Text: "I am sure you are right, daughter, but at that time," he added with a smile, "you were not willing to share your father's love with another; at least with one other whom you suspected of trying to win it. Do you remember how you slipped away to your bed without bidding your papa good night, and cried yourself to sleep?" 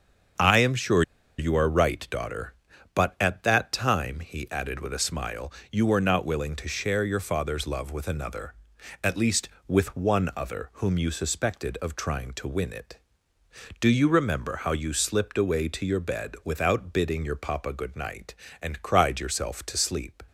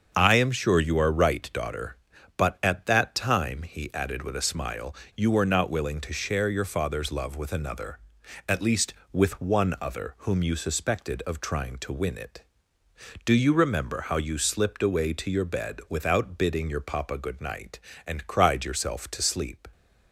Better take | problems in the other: second | starts louder than the rest; until 1.7 s; 7 dB; strong in the second // pauses between "sure" and "you"; slight; at 1.0 s; 0.36 s long

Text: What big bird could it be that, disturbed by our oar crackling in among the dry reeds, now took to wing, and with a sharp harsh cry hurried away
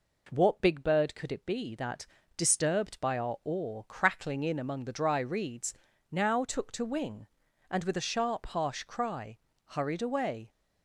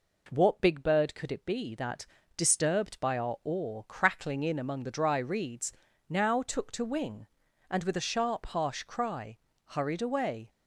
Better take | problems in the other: neither | pauses between "cry" and "hurried"; slight; the same in both

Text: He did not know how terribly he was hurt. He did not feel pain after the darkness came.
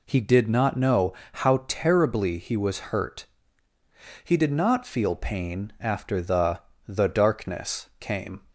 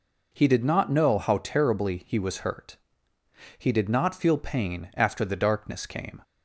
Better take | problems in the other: second | pauses between "know" and "how"; slight; at 1.1 s; 0.20 s long // says "the" twice; at 6.8 s

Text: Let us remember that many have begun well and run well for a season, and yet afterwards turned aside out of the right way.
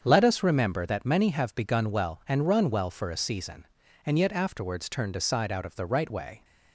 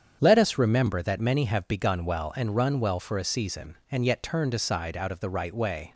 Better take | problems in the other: first | starts louder than the rest; strong; until 1.2 s; 8 dB; strong in the first // skips "afterwards"; at 4.2 s

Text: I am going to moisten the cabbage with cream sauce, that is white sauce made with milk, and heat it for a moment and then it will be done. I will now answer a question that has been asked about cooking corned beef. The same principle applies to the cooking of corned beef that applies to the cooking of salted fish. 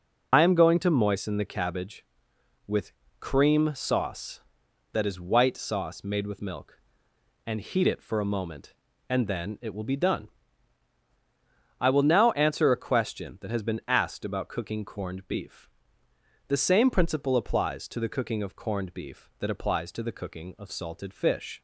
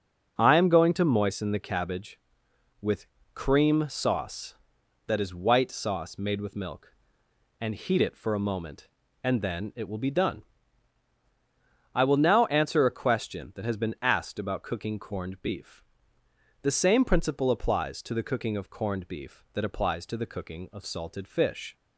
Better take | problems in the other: second | loses the start of "I"; at 0.3 s; 90 ms // pauses between "with" and "cream"; slight; at 2.9 s; 0.28 s long; slight in the second

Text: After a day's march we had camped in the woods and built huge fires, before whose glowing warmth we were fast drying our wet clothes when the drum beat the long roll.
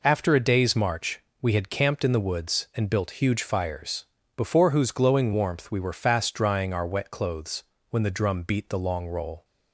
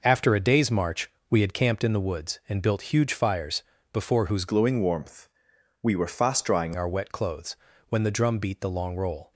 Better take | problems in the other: first | pauses between "march" and "we"; slight; at 1.1 s; 0.18 s long; slight in the first // changes voice from "glowing" to "drying"; from 4.4 to 6.7 s; 2.3 s long // pauses between "warmth" and "we"; noticeable; at 5.2 s; 0.54 s long // pauses between "clothes" and "when"; slight; at 7.5 s; 0.36 s long; slight in the first

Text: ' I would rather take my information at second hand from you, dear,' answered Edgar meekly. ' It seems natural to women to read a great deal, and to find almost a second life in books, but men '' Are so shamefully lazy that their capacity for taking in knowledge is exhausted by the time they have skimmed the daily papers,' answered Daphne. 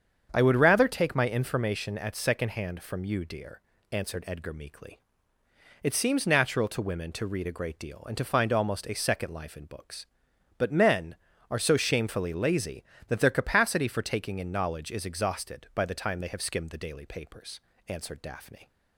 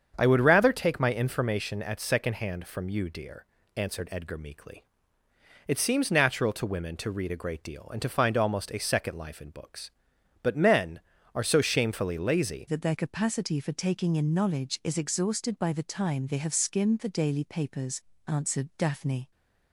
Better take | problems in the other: first | starts louder than the rest; strong; until 1.1 s; 7.5 dB; strong in the first // changes voice at "that"; from 12.6 s on; 6.7 s long

